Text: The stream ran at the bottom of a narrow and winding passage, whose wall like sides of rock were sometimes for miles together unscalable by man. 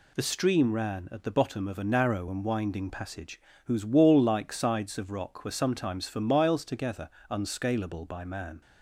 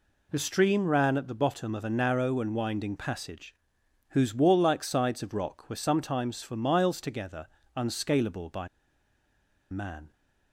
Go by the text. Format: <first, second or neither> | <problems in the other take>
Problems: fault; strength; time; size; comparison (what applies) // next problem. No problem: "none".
first | pauses between "together" and "unscalable"; slight; at 7.4 s; 0.28 s long; slight in the first // pauses between "by" and "man"; at 8.6 s; 1.0 s long